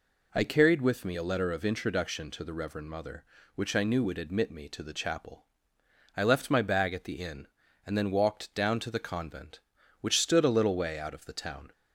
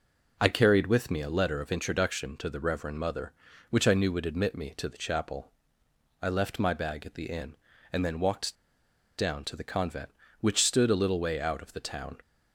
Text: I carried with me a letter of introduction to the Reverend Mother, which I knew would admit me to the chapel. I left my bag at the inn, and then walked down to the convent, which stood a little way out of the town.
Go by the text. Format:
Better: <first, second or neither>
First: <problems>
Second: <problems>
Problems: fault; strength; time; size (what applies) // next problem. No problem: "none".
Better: first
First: none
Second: pauses between "walked" and "down"; noticeable; at 8.5 s; 0.64 s long